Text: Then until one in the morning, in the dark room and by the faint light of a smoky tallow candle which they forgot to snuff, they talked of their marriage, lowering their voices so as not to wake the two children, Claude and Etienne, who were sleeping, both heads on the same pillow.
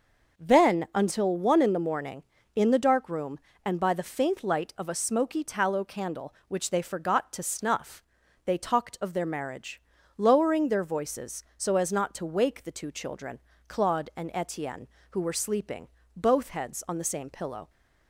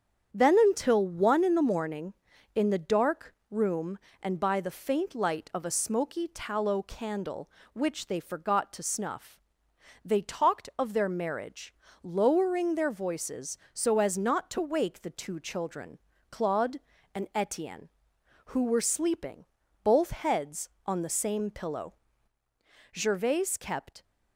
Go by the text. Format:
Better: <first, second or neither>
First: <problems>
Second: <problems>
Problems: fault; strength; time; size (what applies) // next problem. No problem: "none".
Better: first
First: none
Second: starts louder than the rest; strong; until 1.3 s; 8 dB // pauses between "dark" and "room"; slight; at 3.3 s; 0.16 s long // goes on to say "Gervaise kept"; noticeable; from 22.9 s on; 1.1 s long